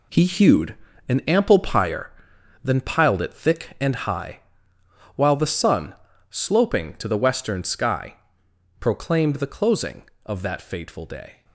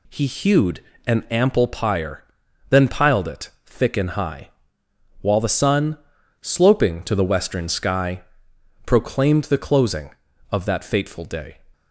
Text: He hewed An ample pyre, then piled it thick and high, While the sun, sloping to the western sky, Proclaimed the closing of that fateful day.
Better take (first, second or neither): second